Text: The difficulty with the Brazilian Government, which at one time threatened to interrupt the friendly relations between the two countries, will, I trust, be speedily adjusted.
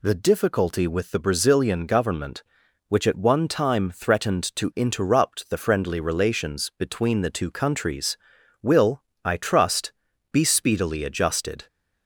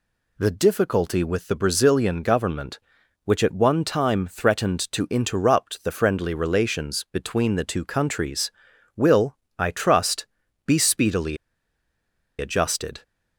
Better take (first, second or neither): first